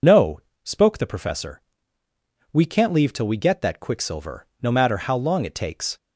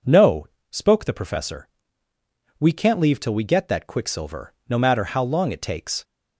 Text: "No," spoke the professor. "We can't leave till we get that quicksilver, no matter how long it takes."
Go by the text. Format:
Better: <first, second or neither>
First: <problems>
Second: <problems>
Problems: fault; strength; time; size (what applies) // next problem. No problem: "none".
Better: second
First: loses the start of "No"; at 0.0 s; 55 ms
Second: none